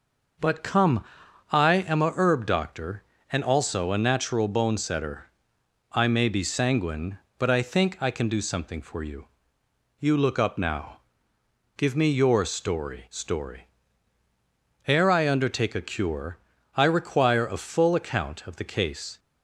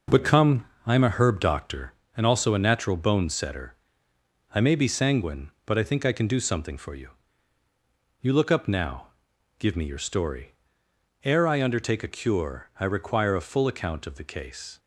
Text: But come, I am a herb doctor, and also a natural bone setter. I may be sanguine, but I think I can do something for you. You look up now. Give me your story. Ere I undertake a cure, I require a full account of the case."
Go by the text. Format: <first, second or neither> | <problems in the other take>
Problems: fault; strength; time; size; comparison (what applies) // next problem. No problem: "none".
second | says "story" twice; at 13.0 s